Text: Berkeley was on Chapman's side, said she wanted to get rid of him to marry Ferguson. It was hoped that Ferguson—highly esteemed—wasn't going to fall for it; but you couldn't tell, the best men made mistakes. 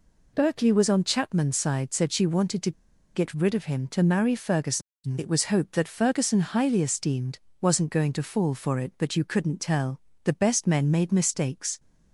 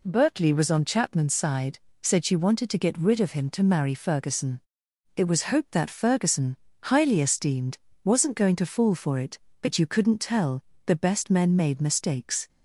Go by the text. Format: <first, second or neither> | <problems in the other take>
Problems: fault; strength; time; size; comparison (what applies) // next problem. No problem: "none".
second | pauses between "to" and "get"; at 2.7 s; 0.44 s long